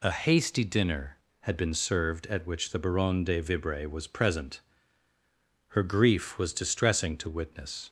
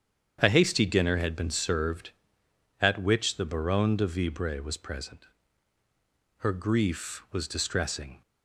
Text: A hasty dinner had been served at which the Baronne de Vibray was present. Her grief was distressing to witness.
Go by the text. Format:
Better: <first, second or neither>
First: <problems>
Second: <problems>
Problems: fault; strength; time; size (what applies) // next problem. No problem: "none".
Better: first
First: none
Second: starts louder than the rest; strong; until 1.4 s; 8.5 dB // stops before "to witness"; at 8.2 s